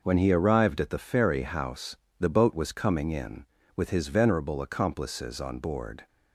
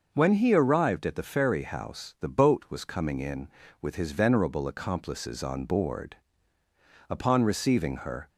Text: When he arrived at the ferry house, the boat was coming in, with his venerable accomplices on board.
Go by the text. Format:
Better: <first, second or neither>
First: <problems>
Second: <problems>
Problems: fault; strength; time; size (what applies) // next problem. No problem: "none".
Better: first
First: none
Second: goes on to say "Upon receiving her"; noticeable; from 7.0 s on; 1.2 s long